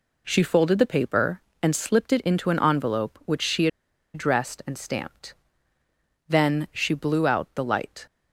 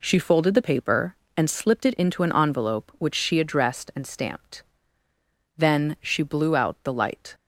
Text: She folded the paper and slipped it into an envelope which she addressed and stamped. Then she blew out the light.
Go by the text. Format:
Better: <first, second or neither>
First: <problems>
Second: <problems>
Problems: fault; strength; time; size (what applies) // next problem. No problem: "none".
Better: second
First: pauses between "she" and "addressed"; noticeable; at 3.6 s; 0.46 s long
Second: none